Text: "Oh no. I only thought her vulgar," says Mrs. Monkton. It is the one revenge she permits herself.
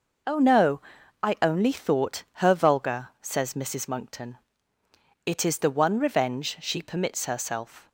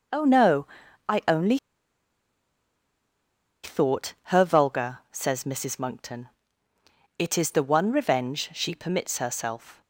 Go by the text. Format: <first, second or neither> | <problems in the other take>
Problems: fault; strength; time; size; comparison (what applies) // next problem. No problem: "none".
first | pauses between "only" and "thought"; strong; at 1.5 s; 2.0 s long // pauses between "thought" and "her"; slight; at 4.1 s; 0.20 s long; slight in the first